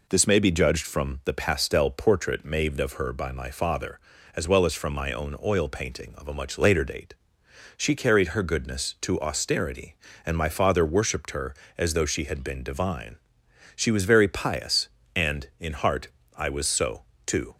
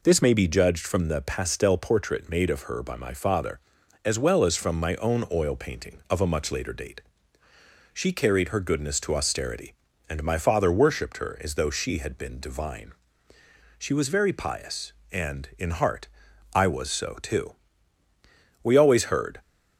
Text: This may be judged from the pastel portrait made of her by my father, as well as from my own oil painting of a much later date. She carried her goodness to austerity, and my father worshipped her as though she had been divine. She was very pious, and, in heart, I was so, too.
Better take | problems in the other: first | goes on to say "We always heard"; noticeable; from 18.6 s on; 0.78 s long

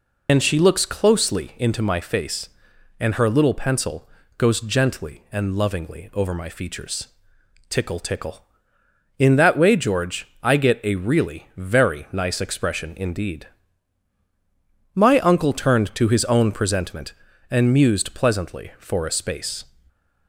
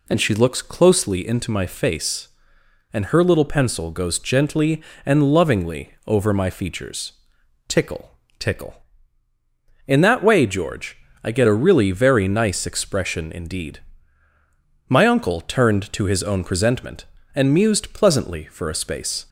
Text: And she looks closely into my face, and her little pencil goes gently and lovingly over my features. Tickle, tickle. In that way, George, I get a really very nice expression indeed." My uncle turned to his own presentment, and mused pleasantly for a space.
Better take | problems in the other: second | loses the start of "And"; at 0.2 s; 100 ms // pauses between "pencil" and "goes"; slight; at 4.0 s; 0.28 s long

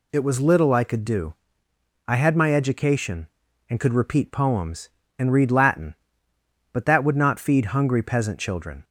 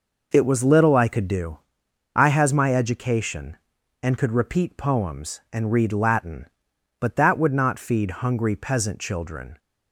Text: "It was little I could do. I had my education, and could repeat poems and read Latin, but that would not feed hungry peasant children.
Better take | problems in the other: first | says "has" for "had"; at 2.2 s

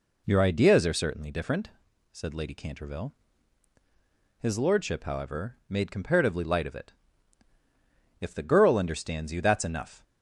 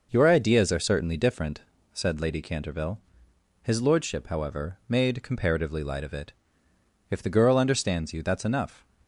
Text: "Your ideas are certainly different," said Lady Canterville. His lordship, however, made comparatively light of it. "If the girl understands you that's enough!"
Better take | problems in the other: neither | none

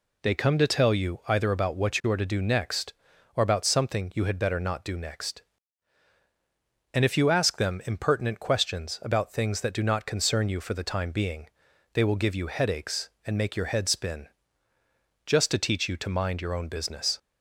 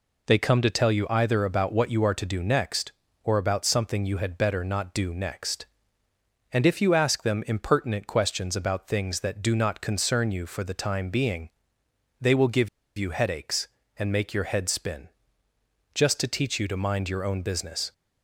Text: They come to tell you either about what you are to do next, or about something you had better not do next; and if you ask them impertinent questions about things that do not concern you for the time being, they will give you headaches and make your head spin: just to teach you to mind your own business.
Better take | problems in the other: first | pauses between "give" and "you"; slight; at 12.6 s; 0.29 s long

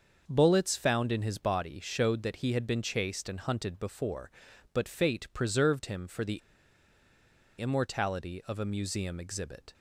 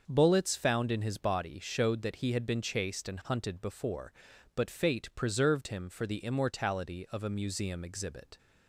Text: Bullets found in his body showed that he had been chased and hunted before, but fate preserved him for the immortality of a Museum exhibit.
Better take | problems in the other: second | starts louder than the rest; until 1.2 s; 6.5 dB; also in the second // pauses between "the" and "immortality"; at 6.3 s; 1.2 s long

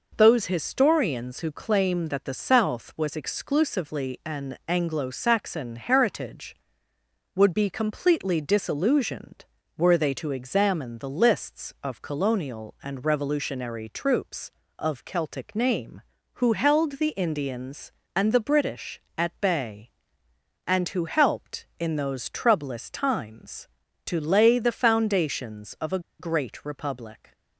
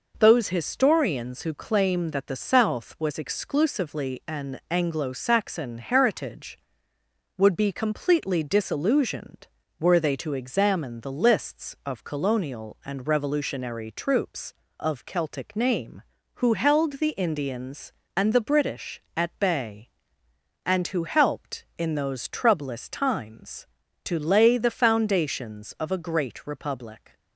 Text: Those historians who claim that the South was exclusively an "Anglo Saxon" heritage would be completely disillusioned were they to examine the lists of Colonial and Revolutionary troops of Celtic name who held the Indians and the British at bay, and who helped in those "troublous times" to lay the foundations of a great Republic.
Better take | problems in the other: second | pauses between "a" and "great"; slight; at 25.9 s; 0.19 s long

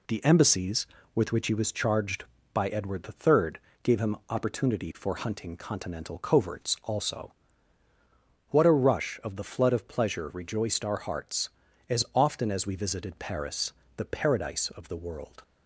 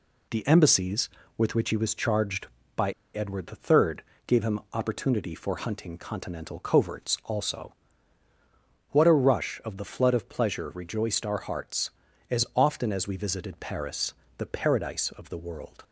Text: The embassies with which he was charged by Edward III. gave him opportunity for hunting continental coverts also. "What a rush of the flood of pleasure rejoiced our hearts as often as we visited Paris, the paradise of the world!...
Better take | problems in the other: first | pauses between "by" and "Edward"; slight; at 2.9 s; 0.24 s long

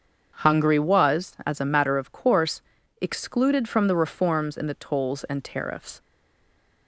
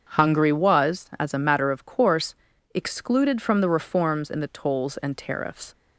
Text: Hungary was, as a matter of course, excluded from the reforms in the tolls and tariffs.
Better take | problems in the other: second | starts louder than the rest; strong; until 1.4 s; 7.5 dB; strong in the second // stays silent after the last word; slight; from 6.0 s on; 0.8 s long

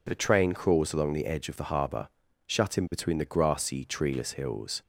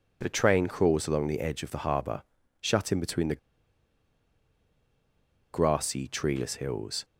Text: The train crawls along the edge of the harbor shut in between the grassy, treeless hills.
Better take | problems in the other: first | pauses between "harbor" and "shut"; at 2.2 s; 0.38 s long; also in the first // pauses between "the" and "grassy"; strong; at 3.3 s; 2.1 s long

